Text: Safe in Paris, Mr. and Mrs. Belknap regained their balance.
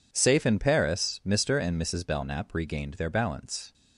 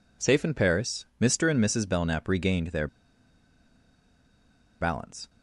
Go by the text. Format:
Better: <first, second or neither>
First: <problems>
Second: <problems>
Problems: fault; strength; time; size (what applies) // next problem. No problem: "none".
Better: first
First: none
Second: pauses between "their" and "balance"; strong; at 2.8 s; 1.9 s long